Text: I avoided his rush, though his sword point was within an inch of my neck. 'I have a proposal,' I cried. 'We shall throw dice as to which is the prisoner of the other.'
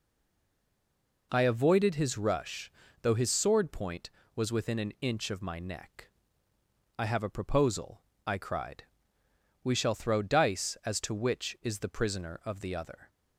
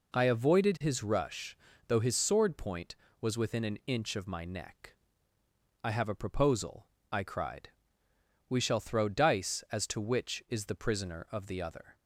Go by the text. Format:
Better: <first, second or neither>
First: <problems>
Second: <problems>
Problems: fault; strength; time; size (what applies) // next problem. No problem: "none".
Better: second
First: stays silent before the first word; noticeable; until 1.3 s; 1.3 s long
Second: none